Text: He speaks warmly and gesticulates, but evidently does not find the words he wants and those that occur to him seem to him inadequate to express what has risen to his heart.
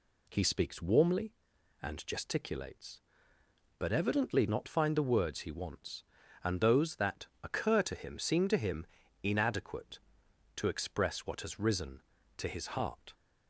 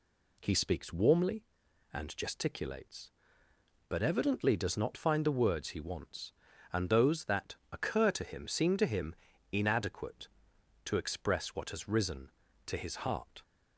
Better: second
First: skips "does"; at 4.4 s // pauses between "that" and "occur"; slight; at 7.2 s; 0.16 s long // pauses between "him" and "inadequate"; slight; at 8.8 s; 0.36 s long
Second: pauses between "that" and "occur"; slight; at 7.5 s; 0.16 s long // pauses between "him" and "inadequate"; slight; at 9.1 s; 0.36 s long

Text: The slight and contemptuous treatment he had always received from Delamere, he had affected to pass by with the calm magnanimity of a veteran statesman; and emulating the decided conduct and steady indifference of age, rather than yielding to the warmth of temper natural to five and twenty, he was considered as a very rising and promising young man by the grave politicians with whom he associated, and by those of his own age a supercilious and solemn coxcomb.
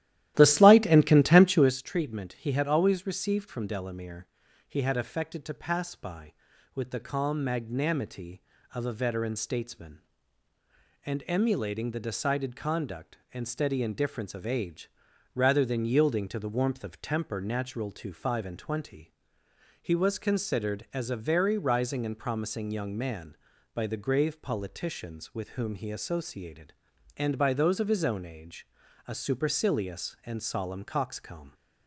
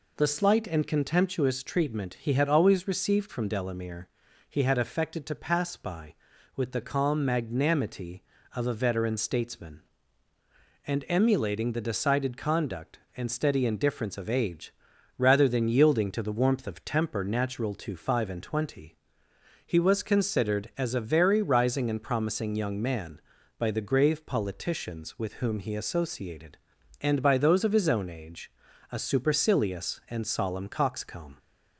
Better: second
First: starts louder than the rest; strong; until 1.8 s; 14 dB // pauses between "age" and "a"; at 28.6 s; 0.40 s long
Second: pauses between "age" and "a"; at 28.4 s; 0.40 s long

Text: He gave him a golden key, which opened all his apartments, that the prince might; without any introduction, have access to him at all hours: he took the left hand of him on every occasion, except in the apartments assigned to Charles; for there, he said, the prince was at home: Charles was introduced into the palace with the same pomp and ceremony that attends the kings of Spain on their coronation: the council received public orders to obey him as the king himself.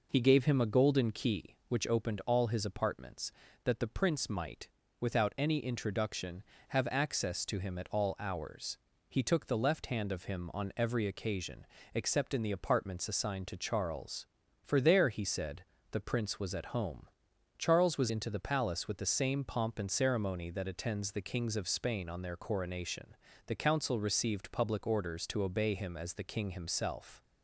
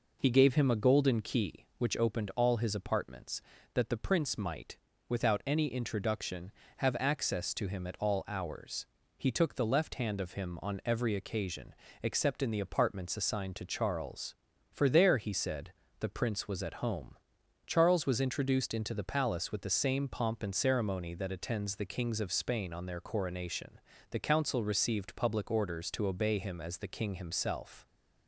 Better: second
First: skips "introduced"; at 18.1 s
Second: none

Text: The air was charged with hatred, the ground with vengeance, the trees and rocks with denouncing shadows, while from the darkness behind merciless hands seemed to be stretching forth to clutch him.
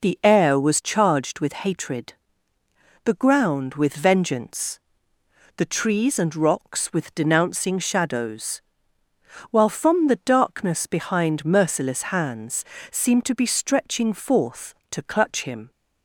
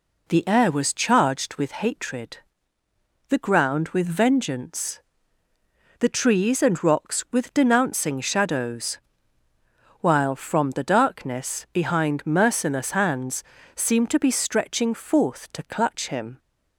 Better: neither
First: pauses between "hands" and "seemed"; slight; at 12.6 s; 0.28 s long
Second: pauses between "hands" and "seemed"; slight; at 13.4 s; 0.32 s long

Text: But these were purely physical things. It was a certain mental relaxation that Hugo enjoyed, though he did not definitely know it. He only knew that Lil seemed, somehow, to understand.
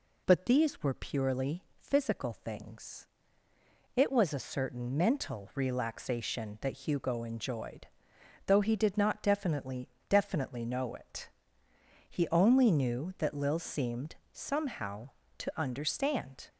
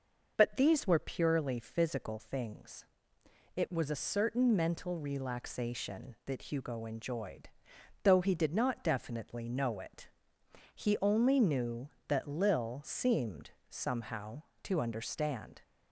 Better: second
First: says "definitely" twice; at 10.0 s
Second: none

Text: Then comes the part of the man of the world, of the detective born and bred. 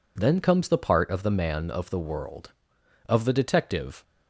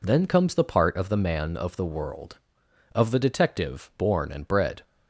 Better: second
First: stops before "born and bred"; at 4.0 s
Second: none

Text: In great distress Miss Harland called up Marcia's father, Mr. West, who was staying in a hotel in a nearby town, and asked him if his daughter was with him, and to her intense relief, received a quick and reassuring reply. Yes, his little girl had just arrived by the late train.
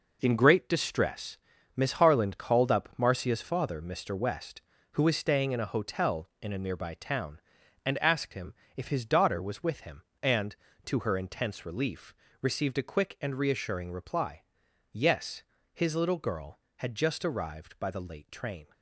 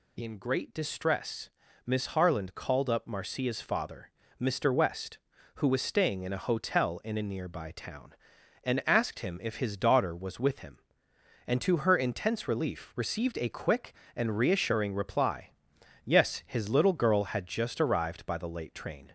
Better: second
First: gets quieter; strong; throughout; 8.5 dB // pauses between "distress" and "Miss"; slight; at 1.3 s; 0.36 s long // pauses between "him" and "if"; slight; at 8.5 s; 0.24 s long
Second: pauses between "distress" and "Miss"; slight; at 1.5 s; 0.34 s long

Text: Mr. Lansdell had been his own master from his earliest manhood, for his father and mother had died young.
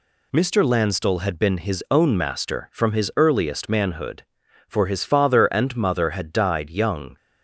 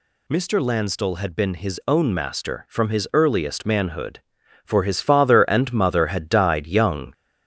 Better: first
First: none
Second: gets louder; slight; throughout; 2.5 dB

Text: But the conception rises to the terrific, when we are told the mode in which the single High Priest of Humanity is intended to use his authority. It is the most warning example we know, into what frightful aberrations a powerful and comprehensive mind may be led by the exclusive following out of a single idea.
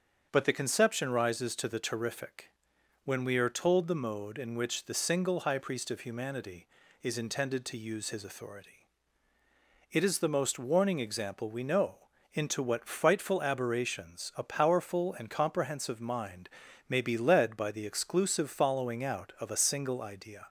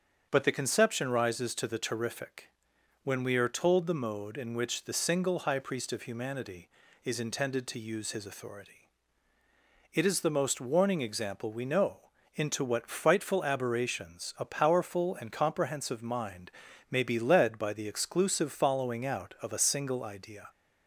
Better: neither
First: starts louder than the rest; strong; until 1.3 s; 7.5 dB // pauses between "mind" and "may"; at 16.4 s; 0.40 s long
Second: starts louder than the rest; strong; until 1.3 s; 7.5 dB // pauses between "mind" and "may"; at 16.4 s; 0.40 s long

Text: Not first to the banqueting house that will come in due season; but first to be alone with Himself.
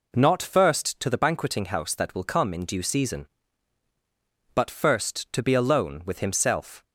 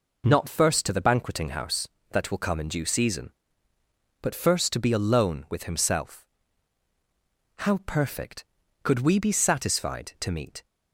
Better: first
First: none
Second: goes on to say "How perfect Could we be satisfied to meet"; strong; from 7.5 s on; 3.0 s long

